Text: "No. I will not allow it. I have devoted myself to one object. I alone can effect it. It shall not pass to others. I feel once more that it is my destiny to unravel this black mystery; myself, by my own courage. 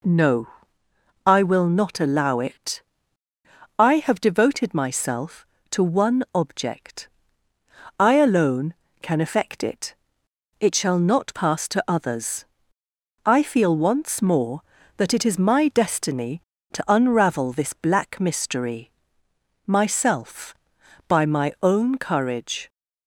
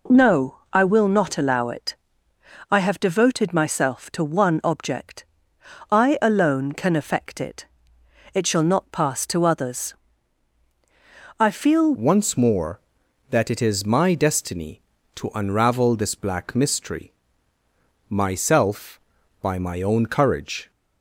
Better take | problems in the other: first | changes voice at "once"; from 11.9 s on; 8.8 s long

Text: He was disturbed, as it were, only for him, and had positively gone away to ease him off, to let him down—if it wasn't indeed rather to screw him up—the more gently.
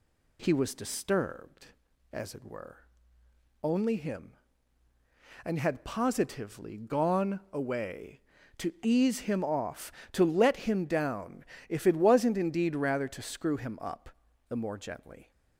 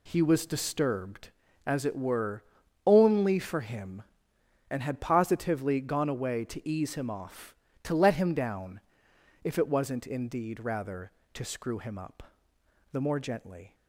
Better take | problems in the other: second | skips "for"; at 3.9 s

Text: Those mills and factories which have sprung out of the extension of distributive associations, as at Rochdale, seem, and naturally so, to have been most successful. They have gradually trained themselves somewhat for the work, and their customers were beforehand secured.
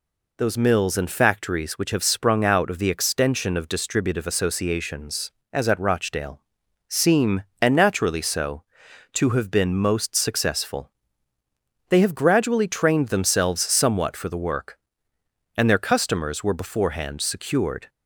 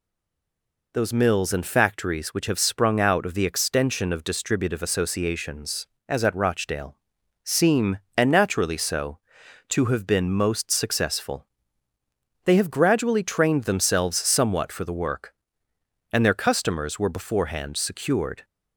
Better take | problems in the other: first | stays silent before the first word; slight; until 0.9 s; 0.9 s long

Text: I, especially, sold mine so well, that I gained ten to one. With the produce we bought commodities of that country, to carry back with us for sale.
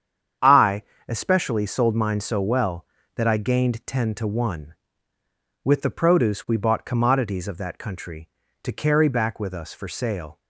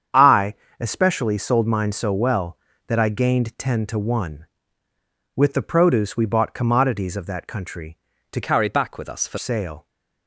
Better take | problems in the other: first | starts louder than the rest; strong; until 1.3 s; 8 dB; strong in the first // changes voice from "carry" to "for"; from 8.4 to 9.3 s; 0.9 s long

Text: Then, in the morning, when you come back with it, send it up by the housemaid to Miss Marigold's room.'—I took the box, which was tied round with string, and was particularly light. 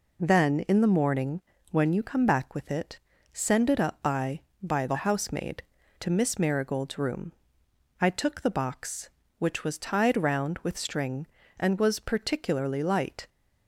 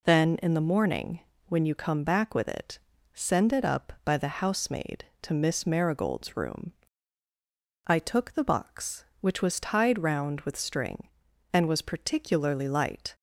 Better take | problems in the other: second | says "by" twice; at 4.6 s

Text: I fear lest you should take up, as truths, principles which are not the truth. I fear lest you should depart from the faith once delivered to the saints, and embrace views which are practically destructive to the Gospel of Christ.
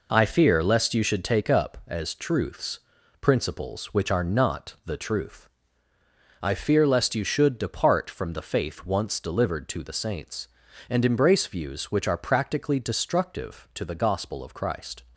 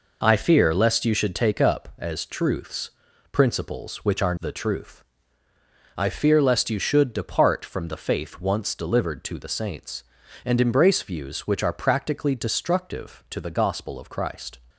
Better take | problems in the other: first | skips "not"; at 4.3 s

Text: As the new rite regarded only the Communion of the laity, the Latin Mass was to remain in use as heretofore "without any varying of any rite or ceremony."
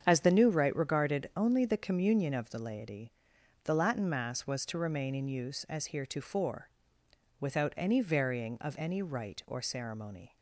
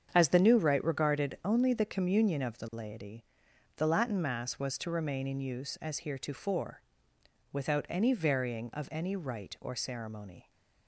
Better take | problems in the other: neither | starts louder than the rest; strong; the same in both // pauses between "heretofore" and "without"; noticeable; the same in both

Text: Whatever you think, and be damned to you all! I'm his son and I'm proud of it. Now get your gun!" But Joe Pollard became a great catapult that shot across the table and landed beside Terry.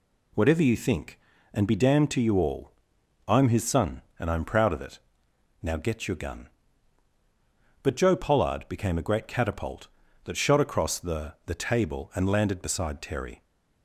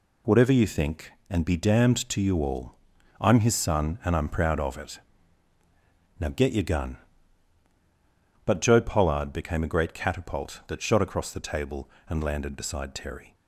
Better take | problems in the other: second | says "the" twice; at 11.4 s

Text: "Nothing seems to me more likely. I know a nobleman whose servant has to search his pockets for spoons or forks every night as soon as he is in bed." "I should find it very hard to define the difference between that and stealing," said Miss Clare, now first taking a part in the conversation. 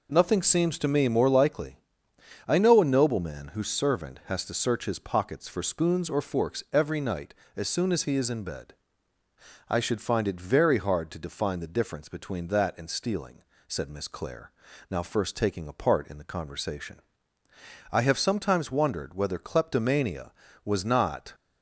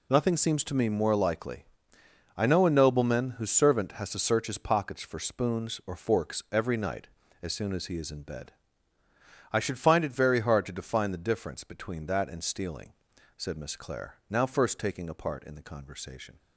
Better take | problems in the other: second | goes on to say "I have sometimes wondered whether kleptomania was not"; strong; from 17.9 s on; 3.4 s long

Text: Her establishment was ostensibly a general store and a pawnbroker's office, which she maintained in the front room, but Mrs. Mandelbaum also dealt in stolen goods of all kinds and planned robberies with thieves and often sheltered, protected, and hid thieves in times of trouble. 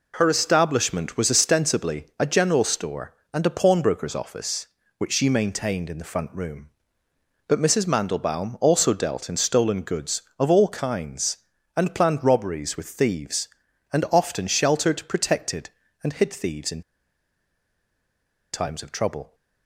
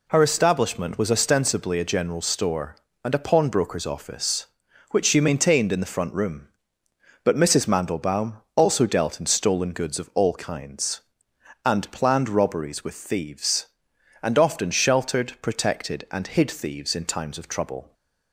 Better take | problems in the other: second | pauses between "in" and "times"; strong; at 16.8 s; 1.7 s long

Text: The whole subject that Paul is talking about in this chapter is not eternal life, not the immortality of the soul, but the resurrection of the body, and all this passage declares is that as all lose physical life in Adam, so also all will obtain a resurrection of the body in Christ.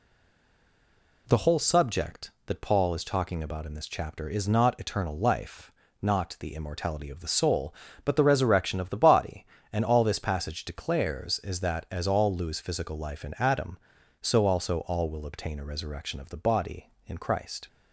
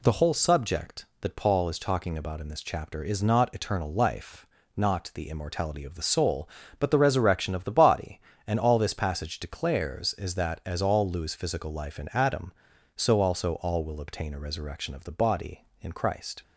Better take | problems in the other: second | stays silent before the first word; noticeable; until 1.2 s; 1.2 s long

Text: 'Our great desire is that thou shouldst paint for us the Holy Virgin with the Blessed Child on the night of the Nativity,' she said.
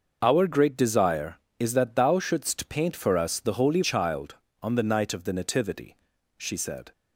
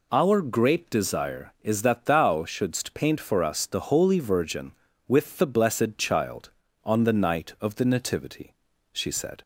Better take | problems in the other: second | skips "Virgin with the Blessed"; at 3.8 s

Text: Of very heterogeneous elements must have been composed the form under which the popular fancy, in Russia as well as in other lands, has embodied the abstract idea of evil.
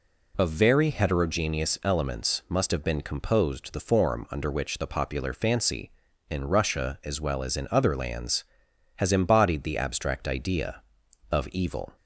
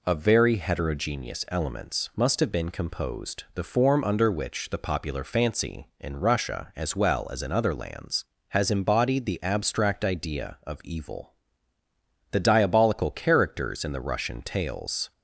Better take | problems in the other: first | goes on to say "The diabolical characters in the Russian tales"; strong; from 12.3 s on; 2.8 s long

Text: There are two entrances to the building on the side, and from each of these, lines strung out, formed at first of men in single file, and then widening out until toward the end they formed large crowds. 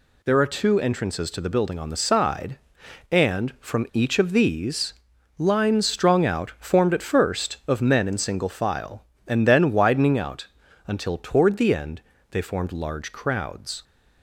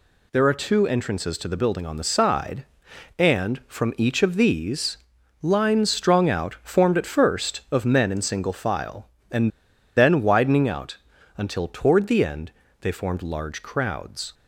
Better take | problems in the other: first | pauses between "and" and "then"; noticeable; at 9.4 s; 0.47 s long // pauses between "out" and "until"; at 10.9 s; 0.40 s long; also in the first // pauses between "end" and "they"; slight; at 12.5 s; 0.30 s long; slight in the first

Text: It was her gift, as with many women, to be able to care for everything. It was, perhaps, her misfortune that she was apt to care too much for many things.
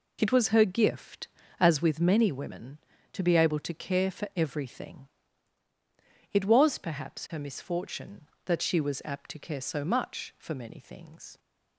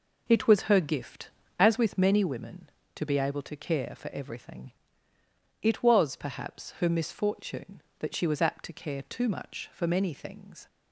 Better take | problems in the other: second | says "so" for "too"; at 9.6 s

